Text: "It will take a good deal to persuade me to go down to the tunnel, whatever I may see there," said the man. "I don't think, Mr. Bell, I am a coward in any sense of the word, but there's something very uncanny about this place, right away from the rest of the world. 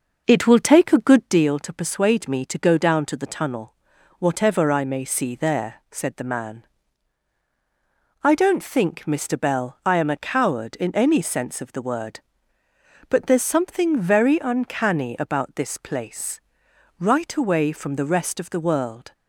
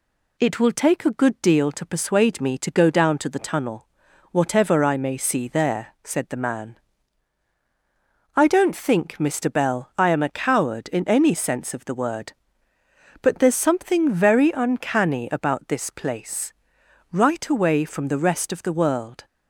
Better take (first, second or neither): second